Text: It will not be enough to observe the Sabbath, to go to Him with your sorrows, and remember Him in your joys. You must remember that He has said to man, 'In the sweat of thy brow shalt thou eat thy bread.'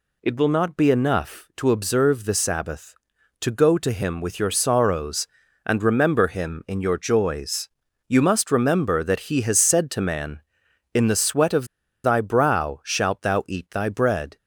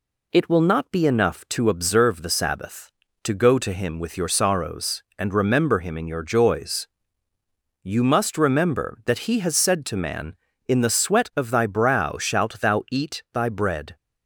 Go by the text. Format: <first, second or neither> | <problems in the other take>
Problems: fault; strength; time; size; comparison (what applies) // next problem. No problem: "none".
second | pauses between "of" and "thy"; at 11.6 s; 0.38 s long